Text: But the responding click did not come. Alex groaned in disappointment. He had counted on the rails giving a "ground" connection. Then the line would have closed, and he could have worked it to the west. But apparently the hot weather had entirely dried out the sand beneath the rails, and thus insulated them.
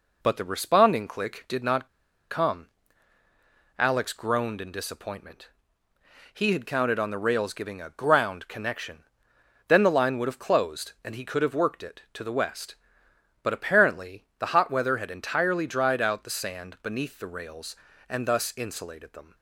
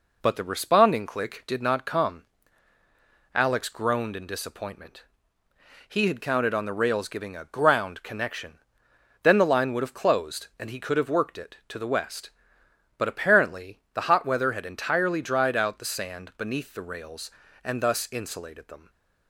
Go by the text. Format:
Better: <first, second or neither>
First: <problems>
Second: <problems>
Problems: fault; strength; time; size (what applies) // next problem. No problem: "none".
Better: second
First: pauses between "not" and "come"; at 1.8 s; 0.42 s long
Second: none